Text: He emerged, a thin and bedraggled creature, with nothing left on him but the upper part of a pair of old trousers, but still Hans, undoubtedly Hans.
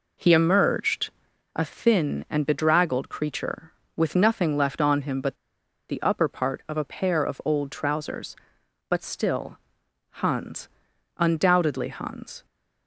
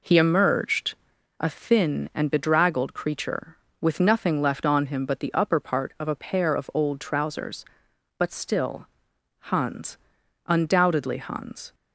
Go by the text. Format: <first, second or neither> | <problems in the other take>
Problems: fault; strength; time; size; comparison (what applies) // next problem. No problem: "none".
second | pauses between "but" and "the"; noticeable; at 5.3 s; 0.53 s long // pauses between "still" and "Hans"; noticeable; at 9.5 s; 0.52 s long; noticeable in the second